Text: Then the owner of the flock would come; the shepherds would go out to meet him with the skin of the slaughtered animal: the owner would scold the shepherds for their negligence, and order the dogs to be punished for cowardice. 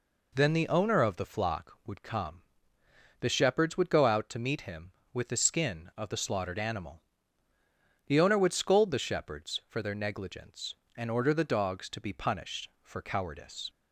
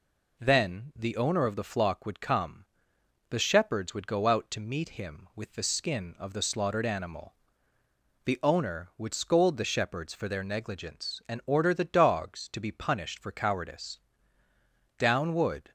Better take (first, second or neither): first